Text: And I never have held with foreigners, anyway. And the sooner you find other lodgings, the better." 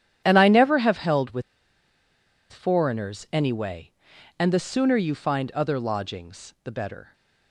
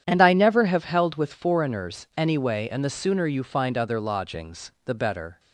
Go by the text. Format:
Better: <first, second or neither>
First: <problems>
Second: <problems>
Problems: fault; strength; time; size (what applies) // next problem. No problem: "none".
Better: second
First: starts louder than the rest; strong; until 1.2 s; 10 dB // pauses between "with" and "foreigners"; at 1.4 s; 1.0 s long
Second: starts louder than the rest; strong; until 1.0 s; 9.5 dB